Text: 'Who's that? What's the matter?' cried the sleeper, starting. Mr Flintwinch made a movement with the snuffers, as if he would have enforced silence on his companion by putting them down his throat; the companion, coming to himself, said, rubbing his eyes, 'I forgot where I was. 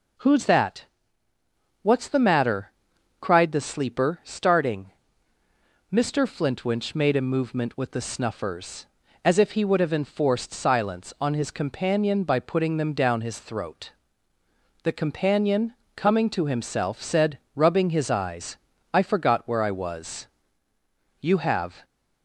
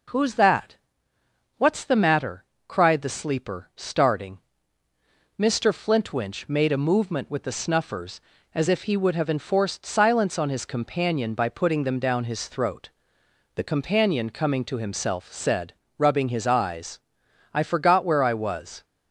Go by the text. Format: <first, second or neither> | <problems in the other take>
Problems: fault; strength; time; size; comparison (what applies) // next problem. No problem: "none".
second | goes on to say "You have"; noticeable; from 21.1 s on; 0.64 s long